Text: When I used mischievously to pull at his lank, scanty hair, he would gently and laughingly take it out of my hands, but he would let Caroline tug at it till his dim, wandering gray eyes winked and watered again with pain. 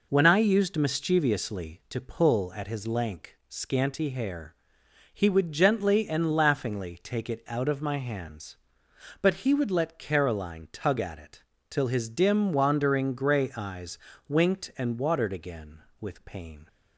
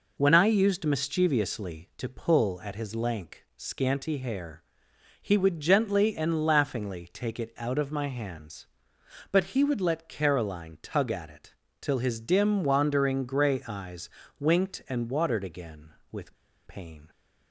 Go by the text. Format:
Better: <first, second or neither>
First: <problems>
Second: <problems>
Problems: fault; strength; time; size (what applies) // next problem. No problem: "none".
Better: first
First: pauses between "it" and "till"; slight; at 11.4 s; 0.30 s long // pauses between "eyes" and "winked"; slight; at 13.9 s; 0.30 s long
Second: pauses between "it" and "till"; slight; at 11.5 s; 0.30 s long // pauses between "eyes" and "winked"; slight; at 14.0 s; 0.30 s long // pauses between "with" and "pain"; slight; at 16.3 s; 0.31 s long